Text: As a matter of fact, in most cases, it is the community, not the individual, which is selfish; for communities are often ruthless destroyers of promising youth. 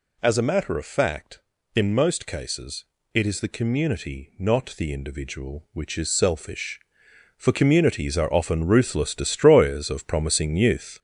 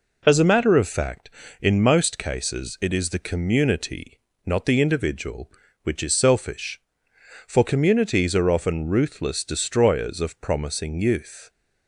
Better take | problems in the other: second | gets louder; noticeable; throughout; 5 dB

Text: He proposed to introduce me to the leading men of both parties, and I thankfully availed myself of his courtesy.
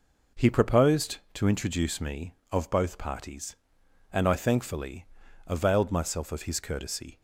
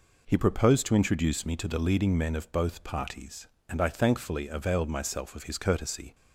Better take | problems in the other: second | skips "to the leading men"; at 2.4 s // pauses between "thankfully" and "availed"; at 5.0 s; 0.40 s long

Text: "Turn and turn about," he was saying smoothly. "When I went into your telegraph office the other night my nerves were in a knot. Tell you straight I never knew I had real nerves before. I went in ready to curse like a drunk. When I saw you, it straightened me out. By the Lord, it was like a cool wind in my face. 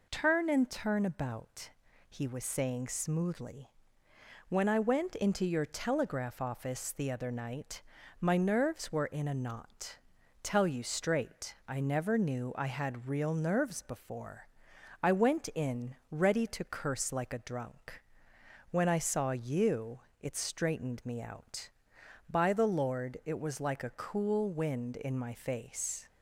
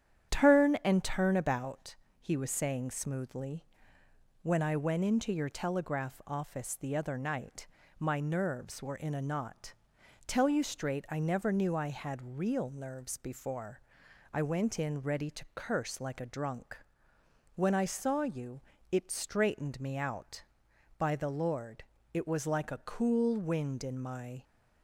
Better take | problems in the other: first | starts louder than the rest; strong; until 1.3 s; 9.5 dB // pauses between "night" and "my"; slight; at 7.6 s; 0.32 s long; slight in the first // stops before "face"; at 24.4 s

